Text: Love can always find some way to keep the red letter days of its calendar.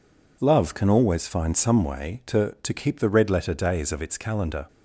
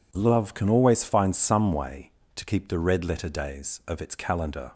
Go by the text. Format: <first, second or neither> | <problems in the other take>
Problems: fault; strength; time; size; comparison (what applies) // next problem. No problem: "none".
second | says "to" twice; at 2.6 s